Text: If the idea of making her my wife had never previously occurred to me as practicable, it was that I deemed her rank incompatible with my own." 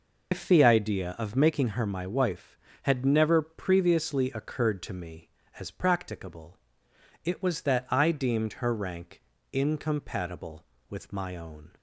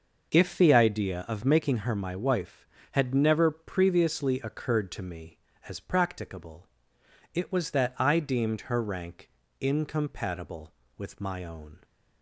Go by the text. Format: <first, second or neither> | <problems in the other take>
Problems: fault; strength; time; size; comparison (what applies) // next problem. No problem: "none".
second | loses the start of "If"; at 0.3 s; 95 ms // pauses between "rank" and "incompatible"; slight; at 9.2 s; 0.32 s long; slight in the second